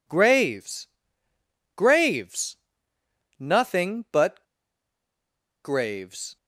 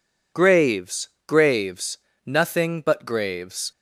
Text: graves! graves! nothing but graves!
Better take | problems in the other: second | pauses between "but" and "graves"; at 4.4 s; 1.1 s long

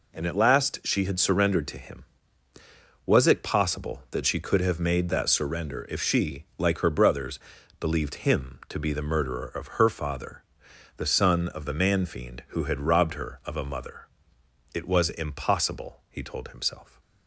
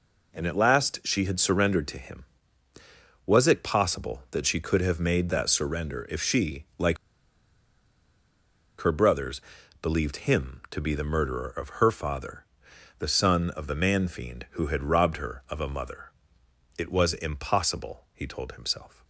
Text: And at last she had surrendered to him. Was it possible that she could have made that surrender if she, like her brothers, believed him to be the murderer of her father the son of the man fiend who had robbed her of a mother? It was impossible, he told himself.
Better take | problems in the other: first | pauses between "like" and "her"; strong; at 6.9 s; 1.8 s long // pauses between "father" and "the"; noticeable; at 12.4 s; 0.60 s long; noticeable in the first

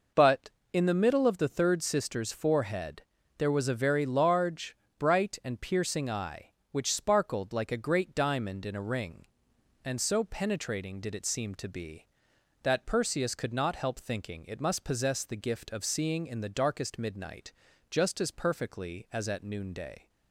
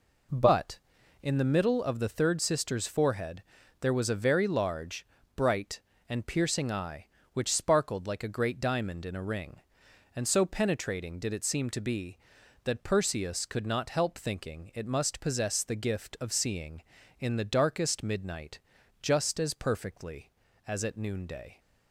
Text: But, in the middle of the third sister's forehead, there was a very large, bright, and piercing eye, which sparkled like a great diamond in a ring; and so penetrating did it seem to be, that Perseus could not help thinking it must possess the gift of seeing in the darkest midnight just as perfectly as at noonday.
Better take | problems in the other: neither | pauses between "midnight" and "just"; the same in both

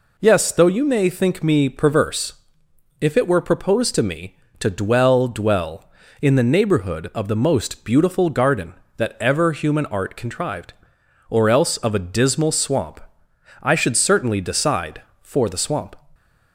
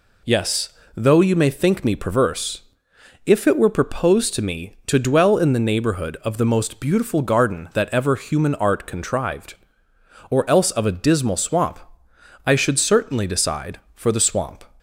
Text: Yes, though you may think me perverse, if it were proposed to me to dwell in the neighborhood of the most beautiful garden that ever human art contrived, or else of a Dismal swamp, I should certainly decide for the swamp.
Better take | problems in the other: second | says "dwell" twice; at 5.2 s

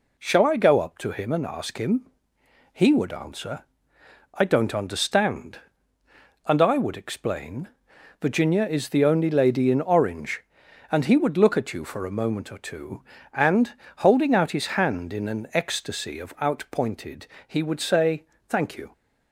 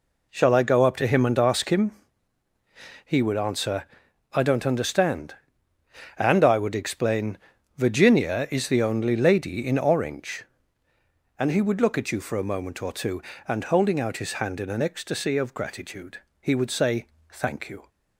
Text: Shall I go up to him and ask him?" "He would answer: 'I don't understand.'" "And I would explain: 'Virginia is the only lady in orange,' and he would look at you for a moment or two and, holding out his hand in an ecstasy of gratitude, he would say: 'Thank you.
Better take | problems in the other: second | says "outpointed" for "gratitude"; at 16.4 s

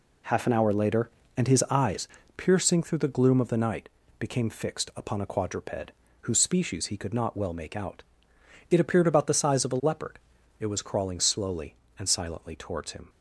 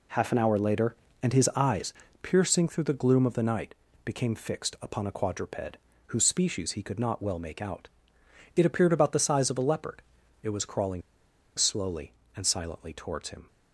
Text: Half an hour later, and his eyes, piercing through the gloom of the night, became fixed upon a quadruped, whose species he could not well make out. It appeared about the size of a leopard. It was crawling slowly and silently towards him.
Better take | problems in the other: first | pauses between "crawling" and "slowly"; noticeable; at 11.0 s; 0.56 s long

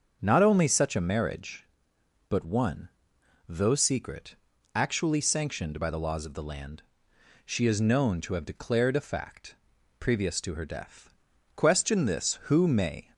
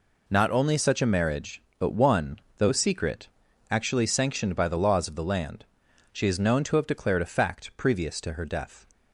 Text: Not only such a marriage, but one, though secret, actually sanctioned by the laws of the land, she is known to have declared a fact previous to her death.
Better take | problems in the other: second | starts louder than the rest; until 1.2 s; 7 dB // pauses between "fact" and "previous"; at 9.5 s; 0.44 s long // goes on to say "Question this who may"; from 11.5 s on; 1.5 s long

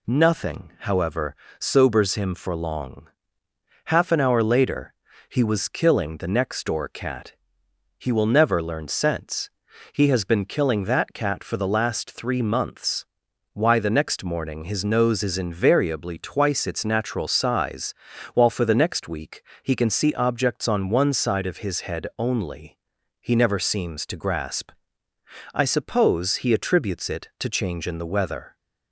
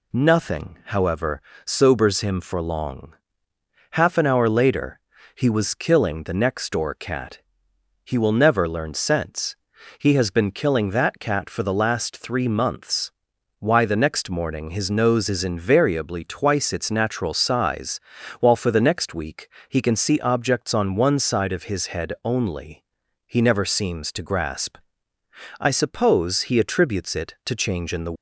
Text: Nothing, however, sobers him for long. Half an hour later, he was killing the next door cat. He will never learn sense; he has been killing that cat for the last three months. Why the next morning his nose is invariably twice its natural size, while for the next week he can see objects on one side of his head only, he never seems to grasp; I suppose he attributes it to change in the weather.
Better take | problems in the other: first | pauses between "week" and "he"; slight; at 19.4 s; 0.22 s long; slight in the first // stops before "weather"; at 28.1 s

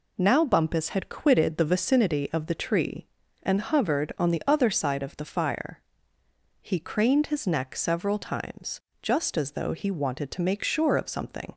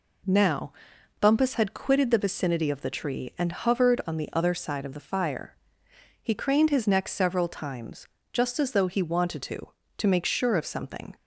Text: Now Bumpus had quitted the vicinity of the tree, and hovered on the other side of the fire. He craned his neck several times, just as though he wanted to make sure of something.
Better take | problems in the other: first | pauses between "Now" and "Bumpus"; noticeable; at 0.7 s; 0.48 s long // says "to" twice; at 9.9 s

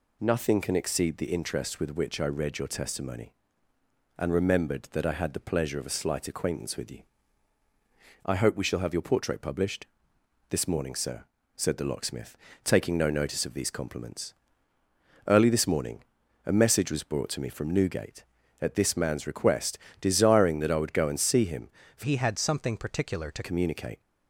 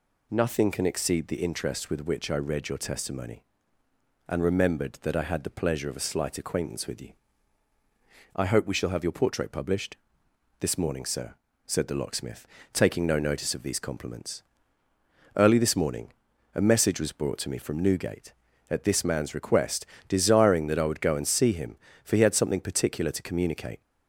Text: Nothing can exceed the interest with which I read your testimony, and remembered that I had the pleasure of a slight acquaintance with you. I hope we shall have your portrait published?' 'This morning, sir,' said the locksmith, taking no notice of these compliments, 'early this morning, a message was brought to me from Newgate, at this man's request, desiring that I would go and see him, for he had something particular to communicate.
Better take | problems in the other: second | changes voice from "he" to "to"; from 22.0 to 23.4 s; 1.4 s long

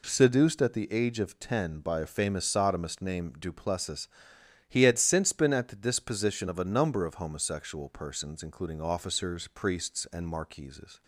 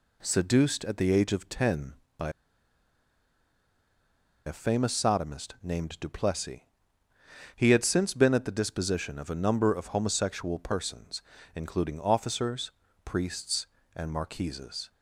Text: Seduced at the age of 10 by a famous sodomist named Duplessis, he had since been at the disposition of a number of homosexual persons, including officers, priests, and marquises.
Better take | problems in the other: first | pauses between "by" and "a"; strong; at 2.2 s; 2.1 s long

